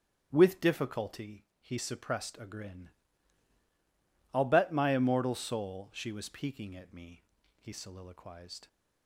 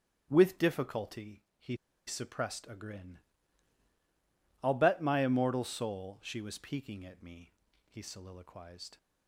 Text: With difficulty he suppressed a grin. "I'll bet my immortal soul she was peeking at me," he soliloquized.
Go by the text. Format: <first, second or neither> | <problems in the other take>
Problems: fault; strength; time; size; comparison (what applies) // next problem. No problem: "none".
first | starts louder than the rest; strong; until 1.3 s; 8 dB; strong in the first // pauses between "difficulty" and "he"; slight; at 1.4 s; 0.16 s long; slight in the first // pauses between "he" and "suppressed"; slight; at 1.7 s; 0.31 s long